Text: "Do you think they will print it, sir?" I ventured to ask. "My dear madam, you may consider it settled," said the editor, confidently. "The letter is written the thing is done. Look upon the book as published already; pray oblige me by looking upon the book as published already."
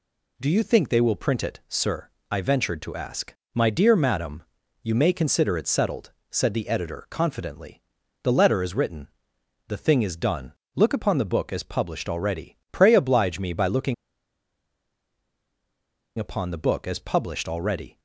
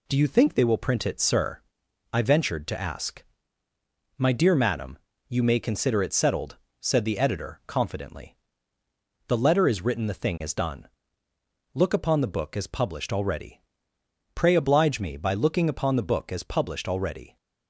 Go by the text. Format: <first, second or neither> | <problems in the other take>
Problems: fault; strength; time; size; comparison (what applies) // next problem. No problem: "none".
second | pauses between "written" and "the"; noticeable; at 9.0 s; 0.62 s long // pauses between "looking" and "upon"; strong; at 13.9 s; 2.2 s long